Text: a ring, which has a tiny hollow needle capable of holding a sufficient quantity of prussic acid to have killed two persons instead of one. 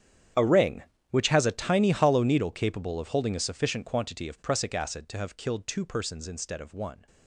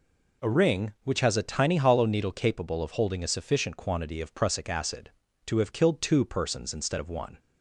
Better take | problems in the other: second | gets quieter; strong; throughout; 19 dB

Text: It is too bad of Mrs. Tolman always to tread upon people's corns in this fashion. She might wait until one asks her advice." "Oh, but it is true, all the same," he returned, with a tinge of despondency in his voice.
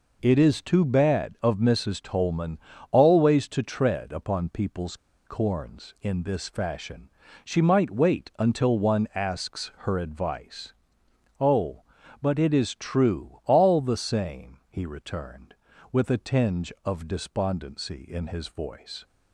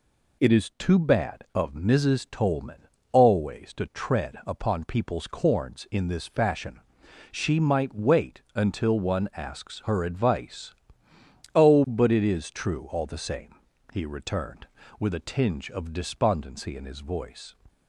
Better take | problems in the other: second | pauses between "Tolman" and "always"; slight; at 2.5 s; 0.32 s long; slight in the second // pauses between "people's" and "corns"; slight; at 4.9 s; 0.31 s long // pauses between "asks" and "her"; slight; at 9.6 s; 0.16 s long

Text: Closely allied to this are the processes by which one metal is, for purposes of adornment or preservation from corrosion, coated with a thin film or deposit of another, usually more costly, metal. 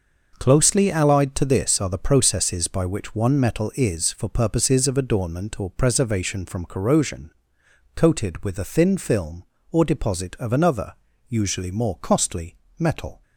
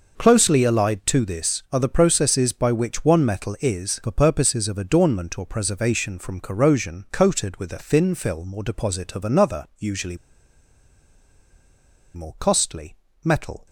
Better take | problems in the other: first | pauses between "usually" and "more"; strong; at 10.1 s; 1.9 s long

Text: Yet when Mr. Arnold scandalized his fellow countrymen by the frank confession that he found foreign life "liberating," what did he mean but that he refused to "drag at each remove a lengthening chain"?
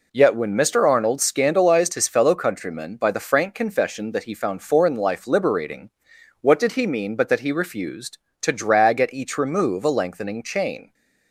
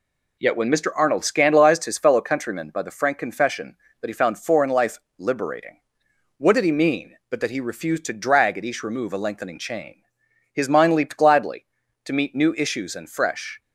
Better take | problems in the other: first | pauses between "life" and "liberating"; slight; at 4.9 s; 0.20 s long // goes on to say "His mind leaped gladly to meet new issues and fresh"; strong; from 10.5 s on; 3.0 s long

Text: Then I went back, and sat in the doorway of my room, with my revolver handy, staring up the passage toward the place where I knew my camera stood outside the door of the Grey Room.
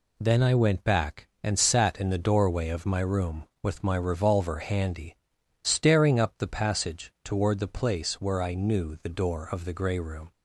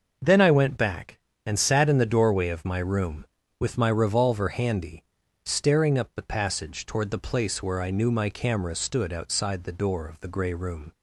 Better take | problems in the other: second | skips "my camera stood outside"; at 8.9 s

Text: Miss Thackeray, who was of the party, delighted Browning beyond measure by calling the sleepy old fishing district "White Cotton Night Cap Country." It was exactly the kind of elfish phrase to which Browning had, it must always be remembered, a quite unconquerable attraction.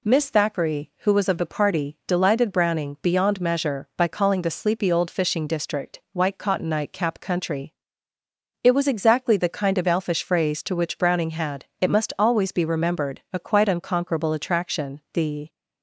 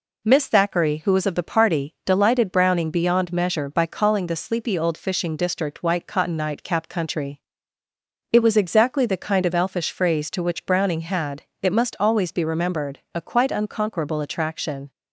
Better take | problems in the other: second | goes on to say "The"; slight; from 15.1 s on; 0.40 s long

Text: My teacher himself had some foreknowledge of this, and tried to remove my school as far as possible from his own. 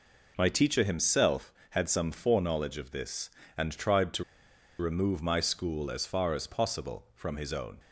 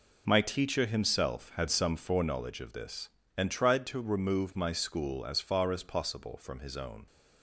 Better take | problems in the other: second | pauses between "to" and "remove"; noticeable; at 4.2 s; 0.56 s long

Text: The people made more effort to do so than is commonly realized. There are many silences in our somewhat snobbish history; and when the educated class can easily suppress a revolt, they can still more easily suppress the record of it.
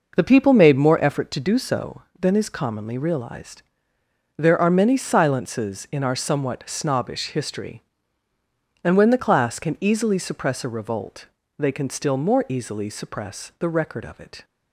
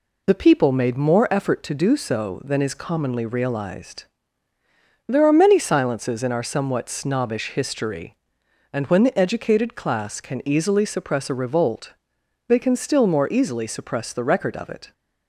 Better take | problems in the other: second | skips "educated"; at 9.2 s

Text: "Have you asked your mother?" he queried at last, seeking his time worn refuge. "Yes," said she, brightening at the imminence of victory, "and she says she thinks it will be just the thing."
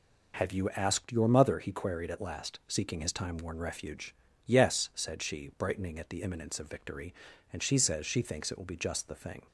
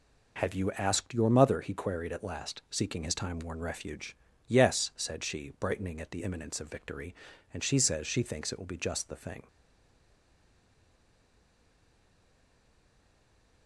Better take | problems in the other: first | stays silent after the last word; strong; from 9.4 s on; 4.2 s long

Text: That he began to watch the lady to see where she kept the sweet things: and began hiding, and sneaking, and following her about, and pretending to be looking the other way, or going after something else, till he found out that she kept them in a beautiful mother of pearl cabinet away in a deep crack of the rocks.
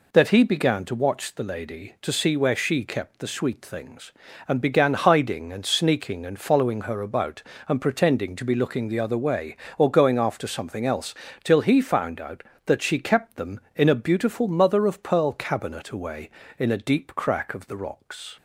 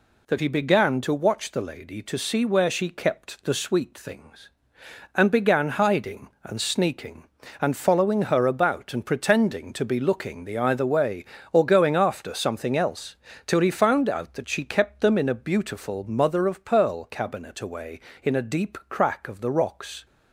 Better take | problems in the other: first | says "either" for "other"; at 10.5 s

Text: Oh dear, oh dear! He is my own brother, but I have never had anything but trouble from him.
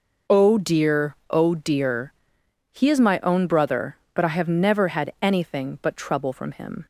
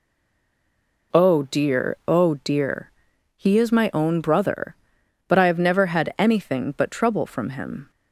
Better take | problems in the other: first | stays silent before the first word; until 1.1 s; 1.1 s long

